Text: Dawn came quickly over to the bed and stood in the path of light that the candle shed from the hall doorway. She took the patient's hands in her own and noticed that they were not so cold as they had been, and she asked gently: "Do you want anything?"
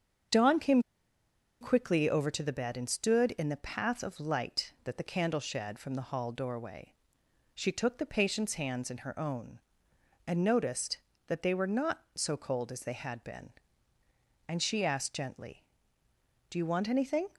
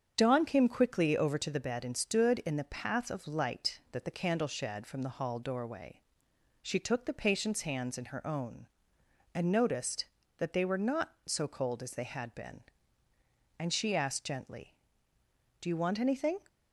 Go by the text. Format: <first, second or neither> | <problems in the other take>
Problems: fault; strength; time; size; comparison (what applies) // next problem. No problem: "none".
second | starts louder than the rest; strong; until 2.1 s; 8 dB; strong in the second // pauses between "came" and "quickly"; noticeable; at 0.8 s; 0.79 s long